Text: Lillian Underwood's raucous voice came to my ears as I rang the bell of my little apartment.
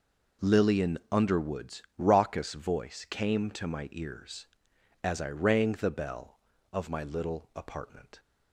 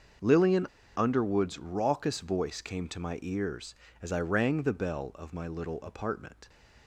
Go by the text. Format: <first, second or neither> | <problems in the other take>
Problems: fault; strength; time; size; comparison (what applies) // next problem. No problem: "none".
first | starts louder than the rest; until 1.5 s; 6.5 dB // pauses between "Lillian" and "Underwood's"; slight; at 0.6 s; 0.30 s long